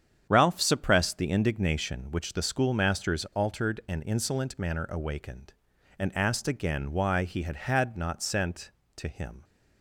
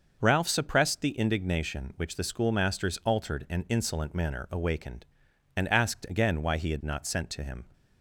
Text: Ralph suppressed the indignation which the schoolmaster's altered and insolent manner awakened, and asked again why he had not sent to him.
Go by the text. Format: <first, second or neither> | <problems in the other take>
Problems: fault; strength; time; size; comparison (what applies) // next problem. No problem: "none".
second | starts louder than the rest; strong; until 1.3 s; 8 dB; noticeable in the second // says "had" twice; at 7.5 s